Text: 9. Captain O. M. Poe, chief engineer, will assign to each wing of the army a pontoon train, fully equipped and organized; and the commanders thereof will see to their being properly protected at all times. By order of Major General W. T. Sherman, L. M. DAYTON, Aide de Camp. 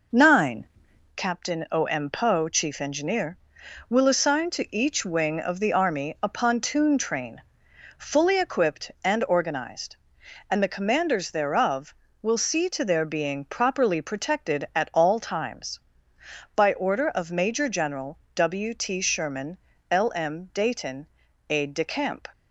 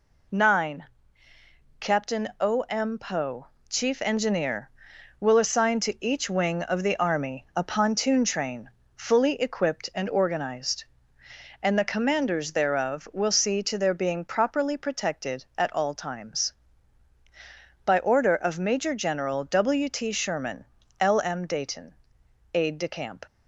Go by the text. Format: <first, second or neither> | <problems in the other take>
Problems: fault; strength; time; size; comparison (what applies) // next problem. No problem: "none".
second | starts louder than the rest; noticeable; until 1.2 s; 5 dB // pauses between "General" and "W"; slight; at 18.1 s; 0.20 s long